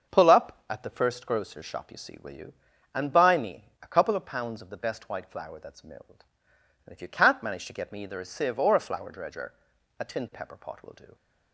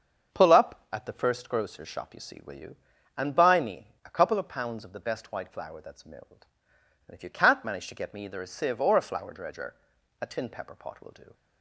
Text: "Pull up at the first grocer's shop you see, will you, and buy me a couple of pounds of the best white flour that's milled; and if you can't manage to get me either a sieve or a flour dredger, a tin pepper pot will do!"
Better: neither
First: starts louder than the rest; until 1.1 s; 6.5 dB // pauses between "me" and "a"; slight; at 3.6 s; 0.18 s long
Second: starts louder than the rest; until 1.3 s; 6.5 dB // pauses between "me" and "a"; slight; at 3.8 s; 0.18 s long

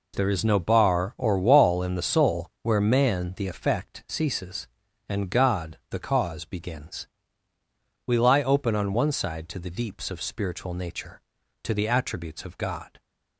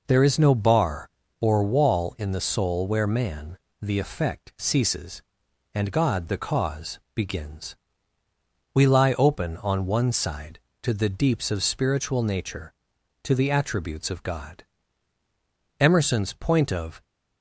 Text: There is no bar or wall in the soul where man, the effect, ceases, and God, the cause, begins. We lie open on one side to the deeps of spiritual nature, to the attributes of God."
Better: first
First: none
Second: goes on to say "Emerson's point of"; noticeable; from 15.7 s on; 1.2 s long

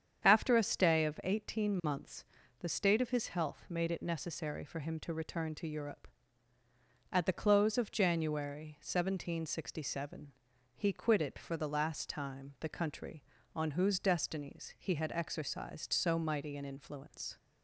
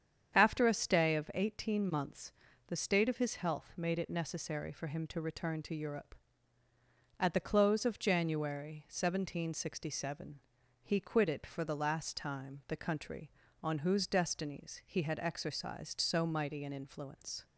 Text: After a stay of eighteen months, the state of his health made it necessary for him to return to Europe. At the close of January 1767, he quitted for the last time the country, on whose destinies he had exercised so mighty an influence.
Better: neither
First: starts louder than the rest; strong; until 1.3 s; 8 dB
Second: starts louder than the rest; strong; until 1.4 s; 8 dB

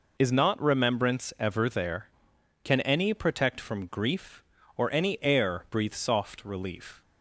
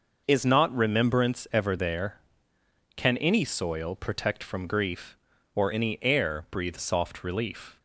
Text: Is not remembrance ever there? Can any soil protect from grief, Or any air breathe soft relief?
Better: second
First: skips "soil"; at 3.1 s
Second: none

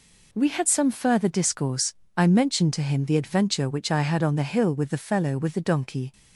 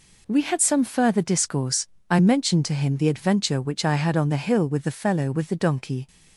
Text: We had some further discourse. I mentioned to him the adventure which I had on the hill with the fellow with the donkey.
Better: neither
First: none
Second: none

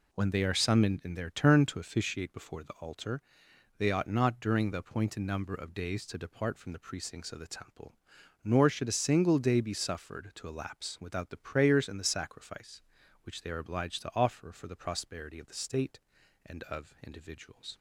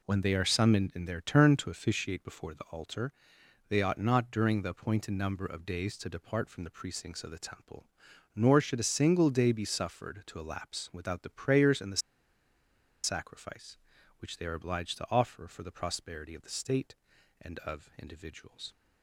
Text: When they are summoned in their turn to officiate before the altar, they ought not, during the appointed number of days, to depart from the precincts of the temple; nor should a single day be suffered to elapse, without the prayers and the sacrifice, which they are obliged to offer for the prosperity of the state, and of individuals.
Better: first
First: none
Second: pauses between "the" and "sacrifice"; at 12.0 s; 1.0 s long

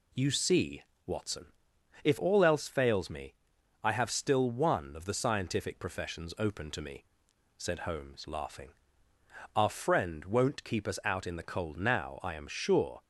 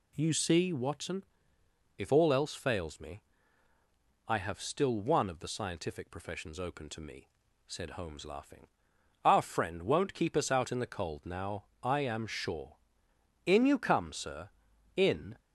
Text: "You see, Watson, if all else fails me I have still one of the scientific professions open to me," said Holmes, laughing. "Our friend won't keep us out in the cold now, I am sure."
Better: first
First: pauses between "me" and "I"; noticeable; at 3.3 s; 0.48 s long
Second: pauses between "me" and "I"; at 3.2 s; 1.0 s long // goes on to say "In you come sir in"; strong; from 13.4 s on; 1.9 s long

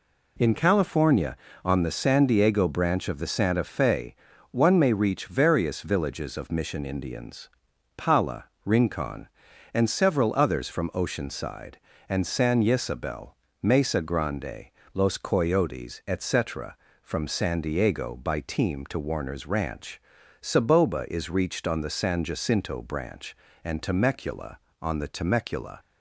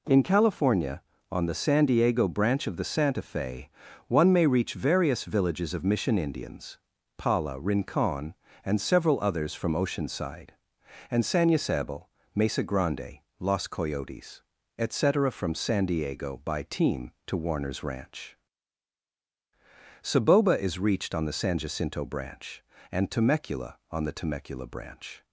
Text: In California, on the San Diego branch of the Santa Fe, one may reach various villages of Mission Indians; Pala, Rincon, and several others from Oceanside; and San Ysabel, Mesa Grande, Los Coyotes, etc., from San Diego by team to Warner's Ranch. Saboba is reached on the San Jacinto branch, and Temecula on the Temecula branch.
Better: second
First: stops before "branch"; at 25.8 s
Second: none

